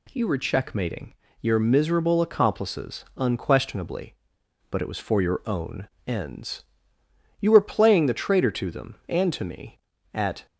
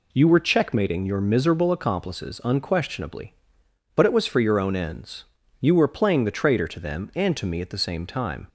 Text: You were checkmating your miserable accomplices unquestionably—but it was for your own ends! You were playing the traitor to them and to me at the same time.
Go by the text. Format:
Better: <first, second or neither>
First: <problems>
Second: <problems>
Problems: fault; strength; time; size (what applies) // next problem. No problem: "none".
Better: second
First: pauses between "checkmating" and "your"; slight; at 1.1 s; 0.26 s long // pauses between "own" and "ends"; slight; at 5.8 s; 0.18 s long // stops before "the same time"; at 10.4 s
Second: none